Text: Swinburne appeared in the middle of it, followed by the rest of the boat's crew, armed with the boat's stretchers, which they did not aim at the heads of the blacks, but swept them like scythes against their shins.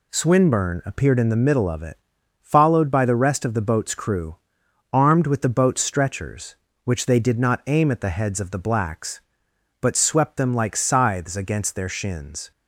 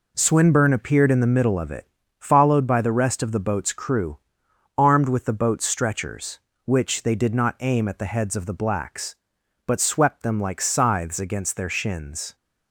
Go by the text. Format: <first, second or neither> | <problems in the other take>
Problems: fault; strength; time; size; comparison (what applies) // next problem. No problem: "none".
neither | none